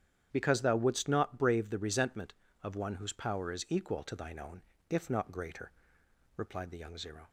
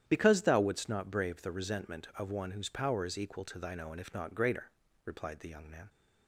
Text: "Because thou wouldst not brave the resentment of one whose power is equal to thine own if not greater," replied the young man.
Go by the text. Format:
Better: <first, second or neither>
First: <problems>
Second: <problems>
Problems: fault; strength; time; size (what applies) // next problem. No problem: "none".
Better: second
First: starts louder than the rest; strong; until 1.3 s; 9.5 dB // pauses between "own" and "if"; slight; at 4.6 s; 0.26 s long // says "zero" for "man"; at 6.9 s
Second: starts louder than the rest; strong; until 1.0 s; 10.5 dB